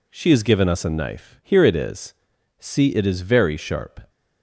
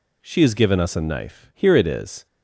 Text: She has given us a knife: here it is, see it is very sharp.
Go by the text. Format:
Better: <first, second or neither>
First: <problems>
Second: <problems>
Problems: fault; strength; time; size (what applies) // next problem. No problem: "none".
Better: first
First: none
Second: stops before "see it is very sharp"; at 2.2 s